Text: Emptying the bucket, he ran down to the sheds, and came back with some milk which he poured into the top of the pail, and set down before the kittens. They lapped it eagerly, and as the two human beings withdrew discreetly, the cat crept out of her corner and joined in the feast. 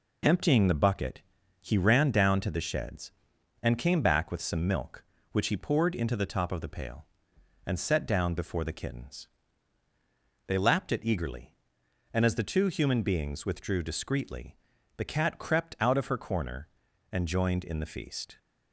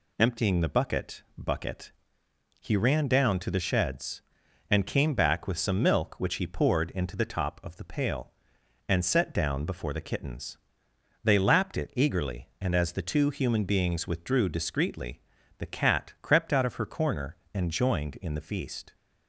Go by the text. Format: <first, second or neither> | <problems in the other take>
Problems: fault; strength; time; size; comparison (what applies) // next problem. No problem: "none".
first | says "bucket" twice; at 1.3 s